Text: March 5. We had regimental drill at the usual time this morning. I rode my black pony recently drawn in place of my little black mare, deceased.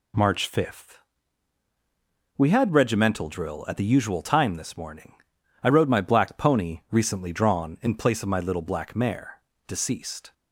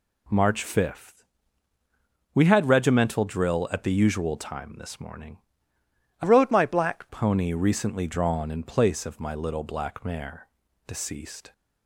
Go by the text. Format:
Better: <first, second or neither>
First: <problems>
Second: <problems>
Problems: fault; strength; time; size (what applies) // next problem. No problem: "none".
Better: first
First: none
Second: changes voice from "rode" to "black"; from 6.2 to 7.0 s; 0.8 s long